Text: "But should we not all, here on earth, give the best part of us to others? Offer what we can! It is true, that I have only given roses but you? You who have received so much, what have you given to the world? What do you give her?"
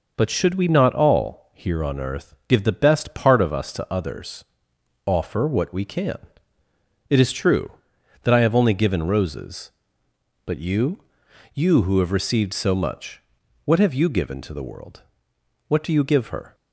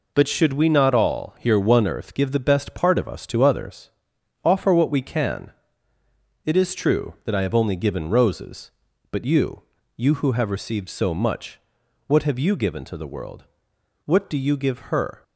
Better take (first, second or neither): first